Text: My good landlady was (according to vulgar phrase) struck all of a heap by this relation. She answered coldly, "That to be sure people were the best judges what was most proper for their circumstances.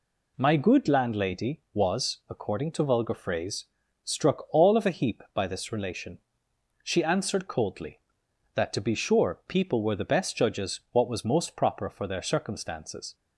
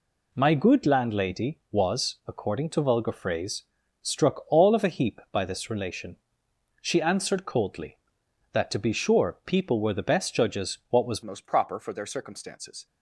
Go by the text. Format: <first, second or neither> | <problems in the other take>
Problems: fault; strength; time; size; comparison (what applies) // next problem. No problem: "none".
first | changes voice at "most"; from 11.2 s on; 1.6 s long